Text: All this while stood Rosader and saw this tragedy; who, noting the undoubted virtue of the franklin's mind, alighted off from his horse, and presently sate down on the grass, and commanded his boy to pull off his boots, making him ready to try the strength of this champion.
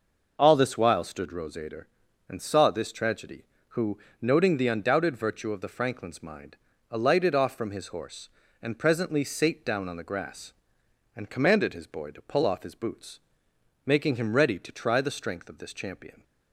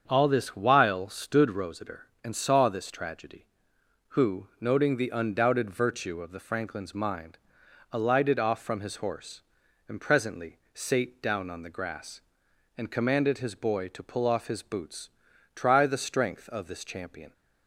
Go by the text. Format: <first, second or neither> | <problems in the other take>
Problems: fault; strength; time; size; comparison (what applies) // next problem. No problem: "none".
first | starts louder than the rest; strong; until 1.0 s; 7 dB // skips "making him ready to"; at 15.3 s